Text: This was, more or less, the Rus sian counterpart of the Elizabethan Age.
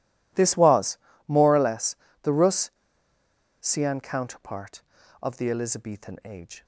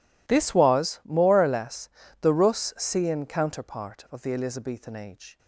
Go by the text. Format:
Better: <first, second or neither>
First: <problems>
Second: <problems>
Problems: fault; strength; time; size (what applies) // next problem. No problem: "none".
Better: second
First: pauses between "Rus" and "sian"; noticeable; at 2.7 s; 0.88 s long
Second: none